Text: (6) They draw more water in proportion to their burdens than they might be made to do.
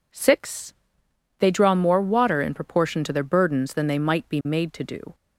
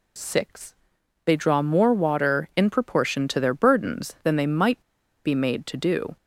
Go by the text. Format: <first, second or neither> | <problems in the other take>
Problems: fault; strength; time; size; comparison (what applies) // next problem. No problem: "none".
first | pauses between "might" and "be"; at 4.8 s; 0.43 s long